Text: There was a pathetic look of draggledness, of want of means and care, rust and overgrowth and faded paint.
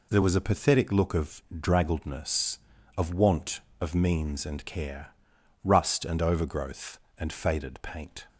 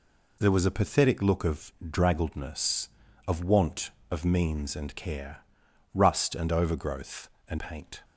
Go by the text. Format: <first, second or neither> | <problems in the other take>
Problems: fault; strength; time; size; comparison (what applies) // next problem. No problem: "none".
first | skips "faded"; at 7.5 s